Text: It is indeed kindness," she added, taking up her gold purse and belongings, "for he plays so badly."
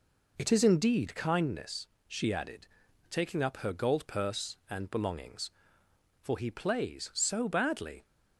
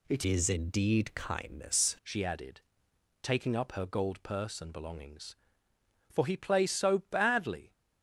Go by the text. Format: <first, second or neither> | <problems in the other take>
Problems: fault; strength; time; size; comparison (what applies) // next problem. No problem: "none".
first | changes voice from "is" to "kindness"; from 0.2 to 1.9 s; 1.7 s long